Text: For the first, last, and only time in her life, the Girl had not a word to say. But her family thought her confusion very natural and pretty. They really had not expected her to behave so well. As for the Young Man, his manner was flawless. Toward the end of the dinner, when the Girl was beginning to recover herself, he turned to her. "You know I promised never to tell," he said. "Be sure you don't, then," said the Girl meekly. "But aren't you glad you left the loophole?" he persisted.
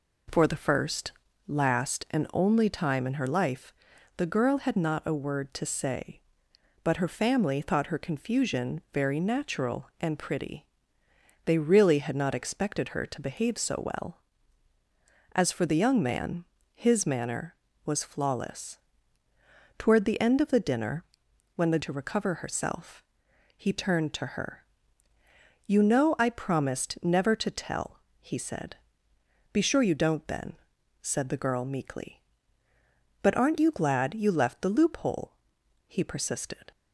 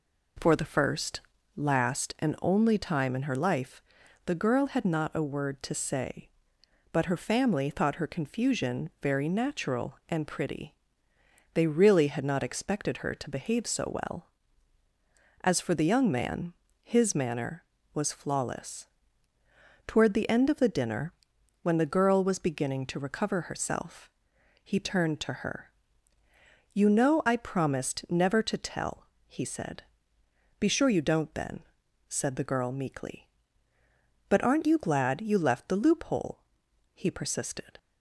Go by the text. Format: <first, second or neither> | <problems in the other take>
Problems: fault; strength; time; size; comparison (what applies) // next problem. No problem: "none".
second | skips "Girl was beginning"; at 21.7 s